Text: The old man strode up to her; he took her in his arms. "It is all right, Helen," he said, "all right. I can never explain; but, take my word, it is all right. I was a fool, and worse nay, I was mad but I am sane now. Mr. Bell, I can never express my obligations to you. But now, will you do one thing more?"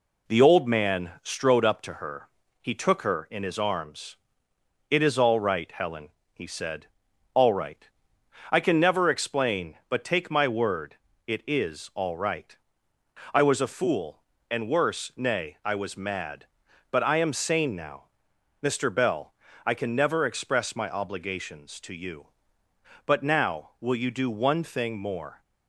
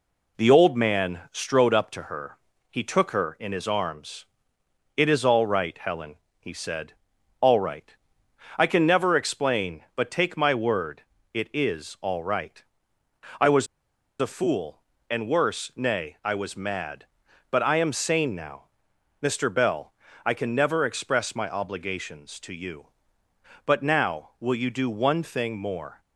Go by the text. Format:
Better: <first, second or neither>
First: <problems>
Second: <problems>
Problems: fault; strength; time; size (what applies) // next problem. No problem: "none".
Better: first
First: none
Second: pauses between "was" and "a"; noticeable; at 13.6 s; 0.55 s long